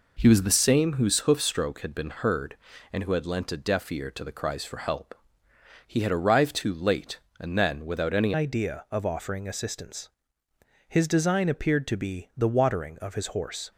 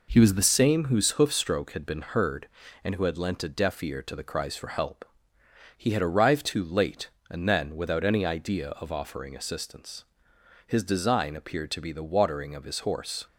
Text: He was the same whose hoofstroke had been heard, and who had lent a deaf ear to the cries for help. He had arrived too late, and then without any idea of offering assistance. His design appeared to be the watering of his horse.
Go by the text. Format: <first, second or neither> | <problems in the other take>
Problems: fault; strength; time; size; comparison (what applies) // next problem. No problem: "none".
second | changes voice at "idea"; from 8.3 s on; 5.4 s long